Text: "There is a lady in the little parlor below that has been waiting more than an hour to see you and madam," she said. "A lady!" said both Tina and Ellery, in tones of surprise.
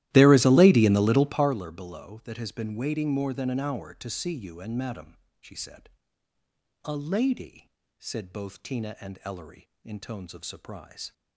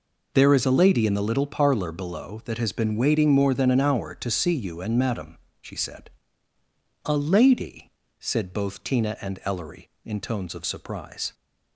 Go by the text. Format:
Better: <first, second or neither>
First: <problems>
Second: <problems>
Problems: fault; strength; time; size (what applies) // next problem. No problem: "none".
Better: second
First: starts louder than the rest; strong; until 1.6 s; 15.5 dB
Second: none